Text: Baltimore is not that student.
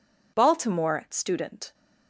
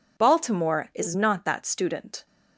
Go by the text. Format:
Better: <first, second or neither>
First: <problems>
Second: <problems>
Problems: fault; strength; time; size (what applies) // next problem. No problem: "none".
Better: second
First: skips "is not that"; at 1.0 s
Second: none